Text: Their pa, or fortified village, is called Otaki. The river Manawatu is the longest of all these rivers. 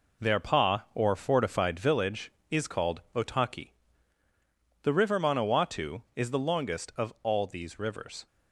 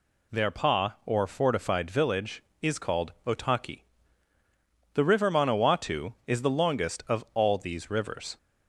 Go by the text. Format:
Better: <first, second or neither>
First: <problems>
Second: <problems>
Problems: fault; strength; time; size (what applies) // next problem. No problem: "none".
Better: second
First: gets quieter; throughout; 7 dB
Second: none